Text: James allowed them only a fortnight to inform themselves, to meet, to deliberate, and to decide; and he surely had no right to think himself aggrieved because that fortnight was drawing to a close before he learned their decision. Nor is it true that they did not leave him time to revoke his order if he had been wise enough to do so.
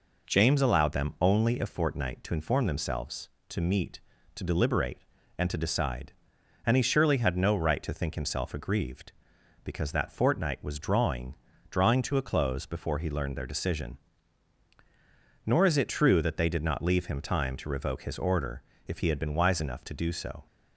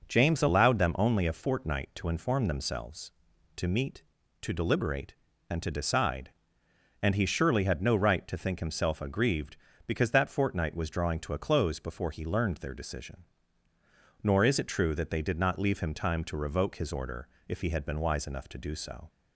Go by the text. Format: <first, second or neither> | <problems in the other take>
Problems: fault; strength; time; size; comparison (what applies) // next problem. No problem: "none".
second | says "drawing" twice; at 11.6 s // pauses between "order" and "if"; slight; at 18.6 s; 0.24 s long; slight in the second